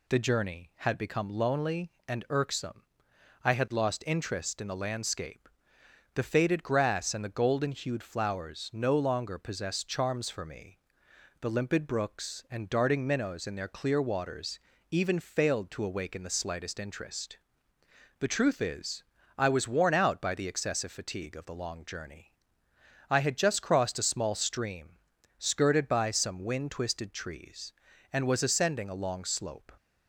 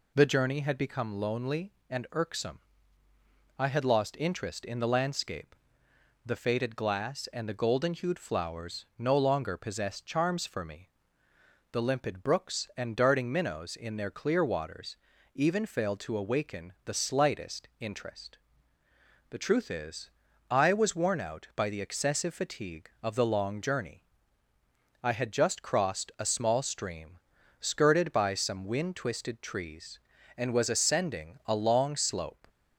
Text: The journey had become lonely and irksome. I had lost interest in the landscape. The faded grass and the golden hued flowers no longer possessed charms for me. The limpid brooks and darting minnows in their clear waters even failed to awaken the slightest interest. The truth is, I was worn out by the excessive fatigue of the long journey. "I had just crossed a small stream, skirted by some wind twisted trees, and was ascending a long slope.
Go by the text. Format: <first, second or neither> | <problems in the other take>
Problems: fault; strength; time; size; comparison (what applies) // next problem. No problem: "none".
first | says "glass" for "grass"; at 6.7 s // pauses between "waters" and "even"; slight; at 14.9 s; 0.36 s long; slight in the first